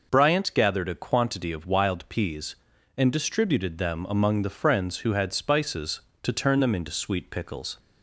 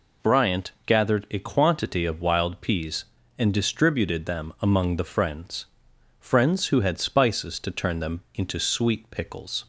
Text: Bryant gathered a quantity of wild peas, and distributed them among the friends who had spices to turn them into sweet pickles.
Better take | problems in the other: first | says "friends" twice; at 6.1 s

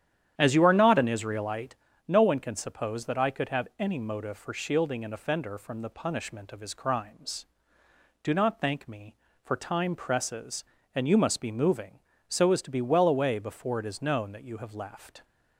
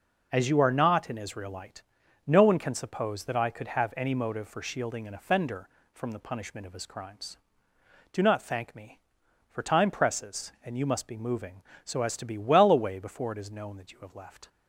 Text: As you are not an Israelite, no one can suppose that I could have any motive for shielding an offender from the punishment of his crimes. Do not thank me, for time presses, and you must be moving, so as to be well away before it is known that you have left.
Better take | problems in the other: second | starts louder than the rest; strong; until 1.9 s; 10 dB

